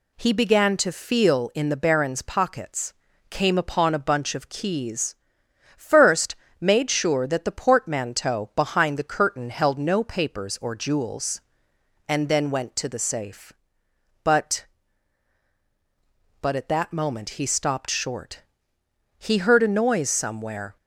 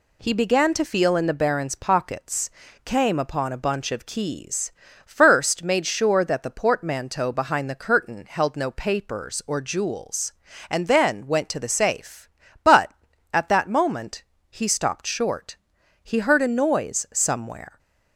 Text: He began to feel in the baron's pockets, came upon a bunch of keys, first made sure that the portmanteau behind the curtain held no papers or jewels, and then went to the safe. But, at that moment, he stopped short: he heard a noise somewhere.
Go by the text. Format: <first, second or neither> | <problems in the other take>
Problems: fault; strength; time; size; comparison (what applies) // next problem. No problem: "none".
second | pauses between "first" and "made"; slight; at 6.3 s; 0.26 s long // says "But" twice; at 16.4 s